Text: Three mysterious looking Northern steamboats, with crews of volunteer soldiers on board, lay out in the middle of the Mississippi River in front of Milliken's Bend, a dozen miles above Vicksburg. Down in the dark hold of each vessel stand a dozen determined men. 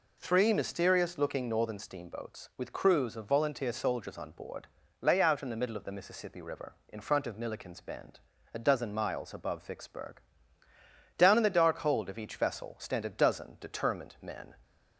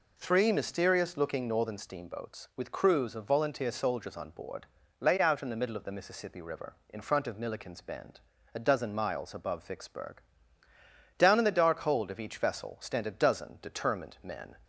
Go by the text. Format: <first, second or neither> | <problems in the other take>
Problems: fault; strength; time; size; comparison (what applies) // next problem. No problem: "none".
neither | none